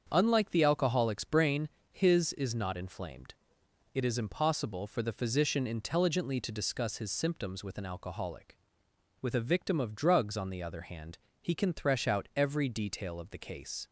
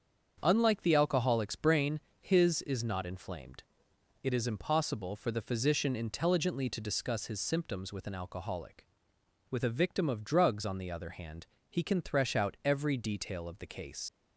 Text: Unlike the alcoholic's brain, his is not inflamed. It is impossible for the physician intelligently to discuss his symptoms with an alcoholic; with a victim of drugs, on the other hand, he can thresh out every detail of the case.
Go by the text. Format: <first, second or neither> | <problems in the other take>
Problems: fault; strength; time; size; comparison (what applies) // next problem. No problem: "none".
first | starts louder than the rest; strong; until 1.4 s; 7 dB; strong in the first // leaves "case" unfinished; at 14.0 s; 55 ms